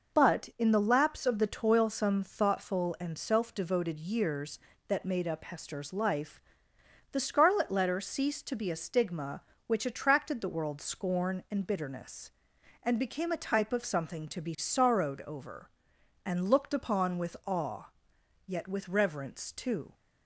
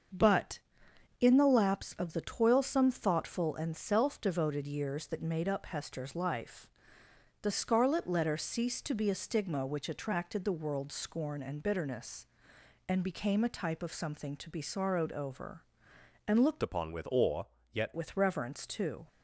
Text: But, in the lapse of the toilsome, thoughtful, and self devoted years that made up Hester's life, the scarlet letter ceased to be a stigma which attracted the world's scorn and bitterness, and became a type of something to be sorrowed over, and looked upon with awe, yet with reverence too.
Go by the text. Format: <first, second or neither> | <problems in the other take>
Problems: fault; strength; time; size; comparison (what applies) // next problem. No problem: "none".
first | starts louder than the rest; until 1.7 s; 6.5 dB // changes voice from "upon" to "yet"; from 16.6 to 17.9 s; 1.3 s long